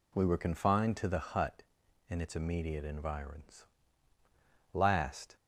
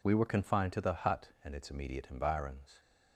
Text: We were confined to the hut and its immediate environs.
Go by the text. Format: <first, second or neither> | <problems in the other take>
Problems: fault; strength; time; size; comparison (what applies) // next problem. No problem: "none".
second | goes on to say "Last"; noticeable; from 4.7 s on; 0.64 s long